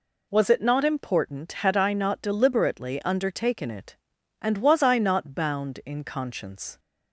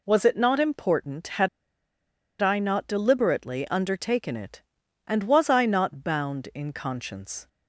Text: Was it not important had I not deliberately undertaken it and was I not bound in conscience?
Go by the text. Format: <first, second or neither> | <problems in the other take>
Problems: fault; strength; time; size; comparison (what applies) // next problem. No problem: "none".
first | pauses between "had" and "I"; noticeable; at 1.4 s; 0.93 s long